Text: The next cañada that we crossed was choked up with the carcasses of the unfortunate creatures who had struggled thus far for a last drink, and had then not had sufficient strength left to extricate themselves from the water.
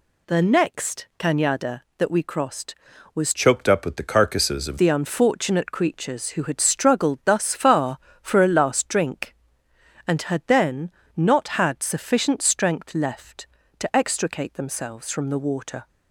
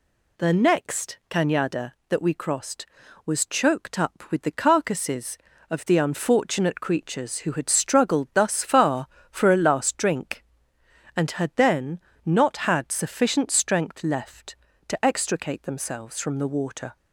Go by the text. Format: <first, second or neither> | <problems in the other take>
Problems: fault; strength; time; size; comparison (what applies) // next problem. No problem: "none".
second | changes voice from "choked" to "of"; from 3.3 to 4.7 s; 1.4 s long // pauses between "then" and "not"; slight; at 10.9 s; 0.26 s long; slight in the second